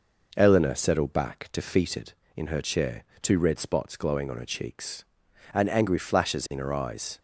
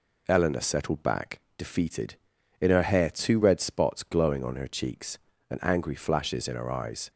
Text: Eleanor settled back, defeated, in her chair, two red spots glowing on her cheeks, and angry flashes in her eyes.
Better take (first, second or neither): first